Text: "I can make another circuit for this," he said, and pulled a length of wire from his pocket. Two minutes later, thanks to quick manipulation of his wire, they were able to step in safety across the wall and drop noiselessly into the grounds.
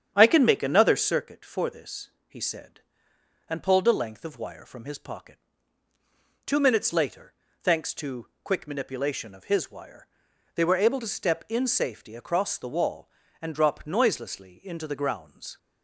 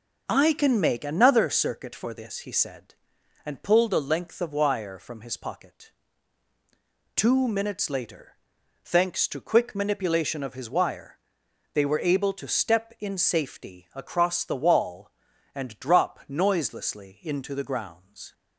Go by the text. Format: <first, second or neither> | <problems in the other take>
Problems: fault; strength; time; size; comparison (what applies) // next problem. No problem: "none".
second | starts louder than the rest; strong; until 1.3 s; 8.5 dB // pauses between "to" and "quick"; slight; at 8.2 s; 0.16 s long